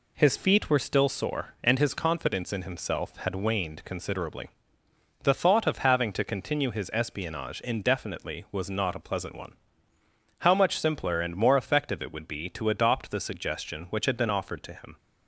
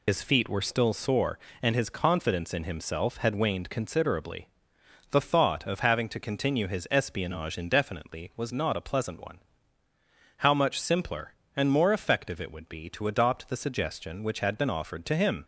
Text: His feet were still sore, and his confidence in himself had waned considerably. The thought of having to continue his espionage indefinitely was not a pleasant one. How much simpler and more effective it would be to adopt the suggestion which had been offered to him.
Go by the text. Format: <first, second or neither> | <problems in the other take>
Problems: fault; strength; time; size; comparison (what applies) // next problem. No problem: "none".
first | loses the start of "His"; at 0.0 s; 85 ms